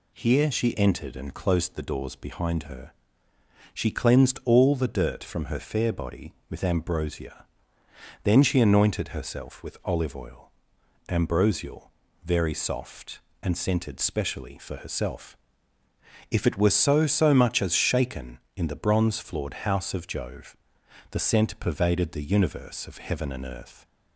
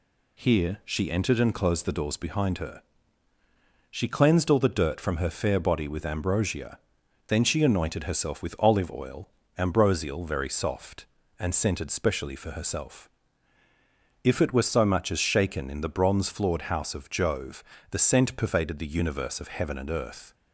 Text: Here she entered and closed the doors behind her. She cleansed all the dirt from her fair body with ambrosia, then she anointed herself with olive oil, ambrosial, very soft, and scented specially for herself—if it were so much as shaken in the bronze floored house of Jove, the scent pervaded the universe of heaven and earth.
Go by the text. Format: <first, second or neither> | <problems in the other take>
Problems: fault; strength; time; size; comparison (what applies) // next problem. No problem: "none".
second | says "so" twice; at 17.0 s